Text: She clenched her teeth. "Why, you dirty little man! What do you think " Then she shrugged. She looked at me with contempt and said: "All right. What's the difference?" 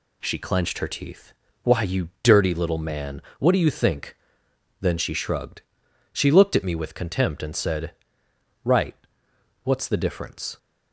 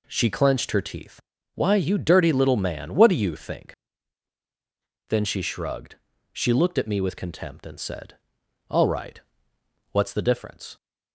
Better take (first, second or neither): second